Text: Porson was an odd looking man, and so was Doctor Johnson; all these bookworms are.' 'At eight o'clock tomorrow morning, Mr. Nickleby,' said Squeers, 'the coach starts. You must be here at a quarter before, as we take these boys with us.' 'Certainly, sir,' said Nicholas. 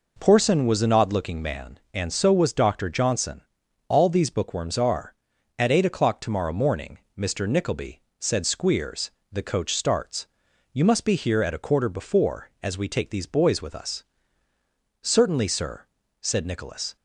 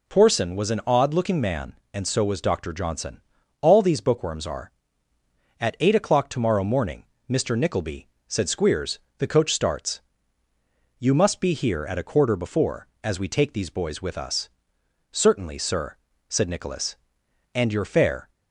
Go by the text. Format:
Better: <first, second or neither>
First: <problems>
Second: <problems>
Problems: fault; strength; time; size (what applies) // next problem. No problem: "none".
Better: first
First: none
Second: goes on to say "And your fare"; noticeable; from 17.5 s on; 0.74 s long